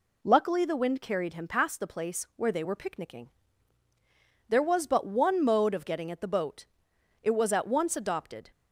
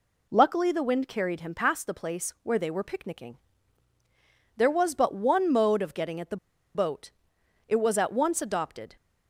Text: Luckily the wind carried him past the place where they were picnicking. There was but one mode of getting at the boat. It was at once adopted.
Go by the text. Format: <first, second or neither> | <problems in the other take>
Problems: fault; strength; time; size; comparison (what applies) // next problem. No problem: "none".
first | pauses between "the" and "boat"; at 6.3 s; 0.39 s long